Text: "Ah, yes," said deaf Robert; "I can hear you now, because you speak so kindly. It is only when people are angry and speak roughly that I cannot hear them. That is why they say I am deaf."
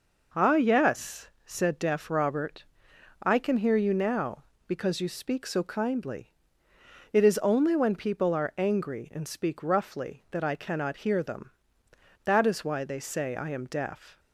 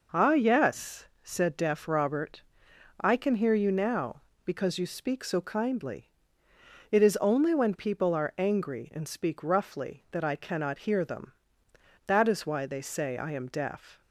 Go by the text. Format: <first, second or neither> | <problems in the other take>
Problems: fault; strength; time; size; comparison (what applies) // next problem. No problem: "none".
neither | none